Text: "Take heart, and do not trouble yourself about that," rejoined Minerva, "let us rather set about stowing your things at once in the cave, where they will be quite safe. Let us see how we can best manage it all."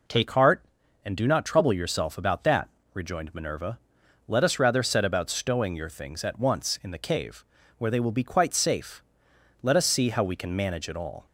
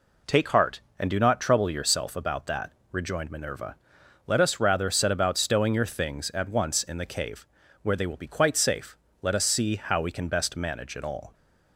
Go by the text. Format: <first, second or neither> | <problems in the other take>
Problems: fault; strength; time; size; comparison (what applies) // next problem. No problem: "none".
second | skips "best"; at 10.5 s